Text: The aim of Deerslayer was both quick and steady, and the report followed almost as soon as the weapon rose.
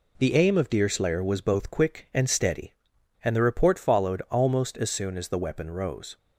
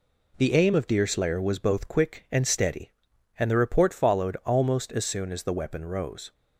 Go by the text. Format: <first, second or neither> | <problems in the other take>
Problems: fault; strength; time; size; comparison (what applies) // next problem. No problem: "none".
neither | none